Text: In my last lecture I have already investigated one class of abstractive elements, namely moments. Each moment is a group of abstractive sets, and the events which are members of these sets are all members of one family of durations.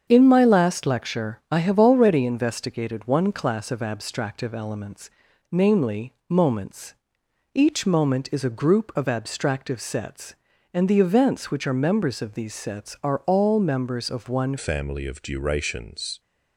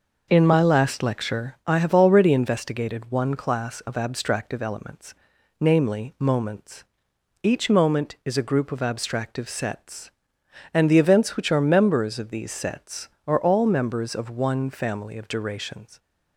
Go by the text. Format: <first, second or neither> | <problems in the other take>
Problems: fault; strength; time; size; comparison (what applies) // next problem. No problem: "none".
second | starts louder than the rest; strong; until 1.1 s; 7.5 dB // pauses between "namely" and "moments"; slight; at 6.1 s; 0.16 s long // changes voice at "family"; from 14.5 s on; 1.6 s long